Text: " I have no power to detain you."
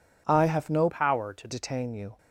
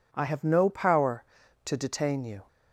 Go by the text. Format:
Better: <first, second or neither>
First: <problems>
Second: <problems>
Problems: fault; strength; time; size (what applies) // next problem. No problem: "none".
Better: second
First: changes voice from "power" to "to"; from 0.8 to 1.4 s; 0.6 s long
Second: none